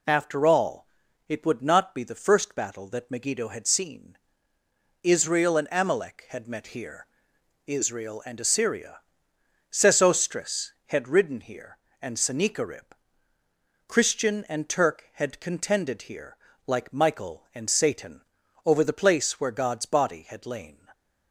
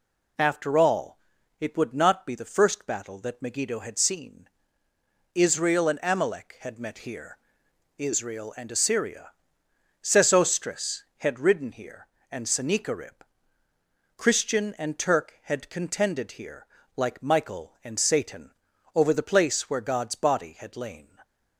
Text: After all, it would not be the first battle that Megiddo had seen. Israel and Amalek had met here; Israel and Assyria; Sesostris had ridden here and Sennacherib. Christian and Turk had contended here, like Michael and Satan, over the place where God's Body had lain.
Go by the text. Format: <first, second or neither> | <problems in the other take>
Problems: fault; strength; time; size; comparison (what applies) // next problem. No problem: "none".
neither | none